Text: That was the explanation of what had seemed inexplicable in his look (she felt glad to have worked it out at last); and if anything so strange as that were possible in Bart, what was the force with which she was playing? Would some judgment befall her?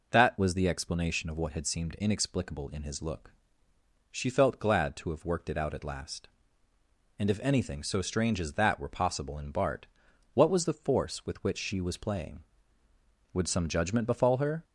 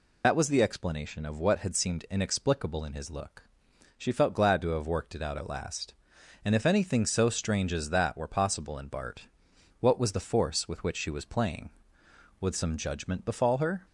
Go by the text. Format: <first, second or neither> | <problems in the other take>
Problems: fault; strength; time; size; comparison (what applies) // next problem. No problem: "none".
first | loses the start of "That"; at 0.2 s; 75 ms